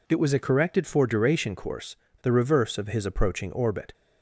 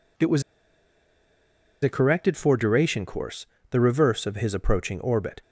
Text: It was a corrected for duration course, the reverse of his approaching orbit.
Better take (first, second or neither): first